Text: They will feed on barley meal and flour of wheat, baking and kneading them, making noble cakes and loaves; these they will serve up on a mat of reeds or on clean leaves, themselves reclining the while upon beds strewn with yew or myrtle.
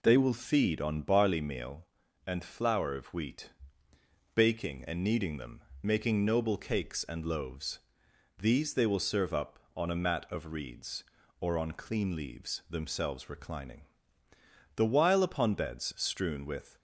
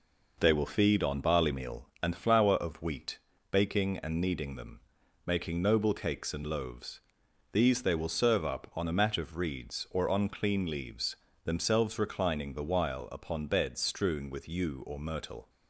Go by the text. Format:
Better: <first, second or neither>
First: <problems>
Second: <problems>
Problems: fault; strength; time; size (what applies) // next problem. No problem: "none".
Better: second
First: pauses between "reclining" and "the"; noticeable; at 13.8 s; 0.90 s long // stops before "yew or myrtle"; at 16.7 s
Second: none